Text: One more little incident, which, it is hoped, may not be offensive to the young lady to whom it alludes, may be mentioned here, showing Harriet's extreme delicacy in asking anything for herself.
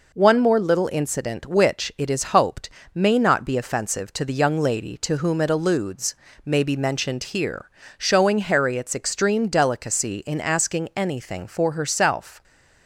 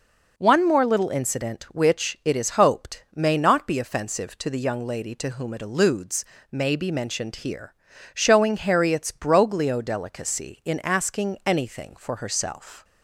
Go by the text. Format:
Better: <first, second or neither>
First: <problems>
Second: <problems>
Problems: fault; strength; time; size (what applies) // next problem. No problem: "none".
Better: first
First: none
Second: says "broglio" for "extreme"; at 9.1 s